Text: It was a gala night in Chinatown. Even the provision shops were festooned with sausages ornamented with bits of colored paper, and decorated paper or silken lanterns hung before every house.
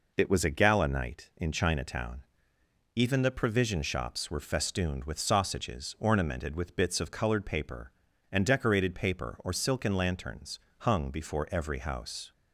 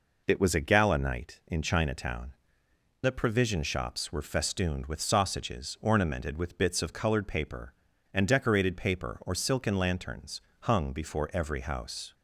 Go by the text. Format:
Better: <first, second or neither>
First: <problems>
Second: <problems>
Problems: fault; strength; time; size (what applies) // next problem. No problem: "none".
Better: first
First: pauses between "lanterns" and "hung"; slight; at 10.5 s; 0.20 s long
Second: skips "Even"; at 2.6 s // pauses between "lanterns" and "hung"; slight; at 10.4 s; 0.20 s long